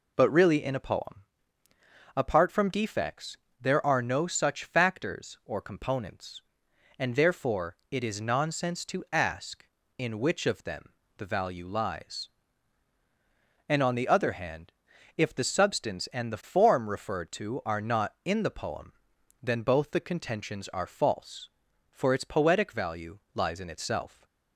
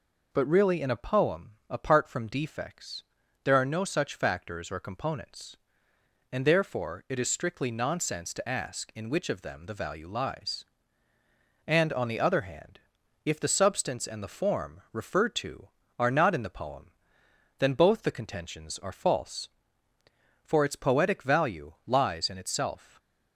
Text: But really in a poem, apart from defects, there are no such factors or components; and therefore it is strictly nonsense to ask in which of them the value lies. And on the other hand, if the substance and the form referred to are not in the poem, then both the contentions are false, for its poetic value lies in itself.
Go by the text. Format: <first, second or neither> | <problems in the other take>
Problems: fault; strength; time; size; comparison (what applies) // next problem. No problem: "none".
second | skips "strictly"; at 8.1 s // pauses between "them" and "the"; slight; at 10.8 s; 0.28 s long // pauses between "value" and "lies"; slight; at 23.1 s; 0.16 s long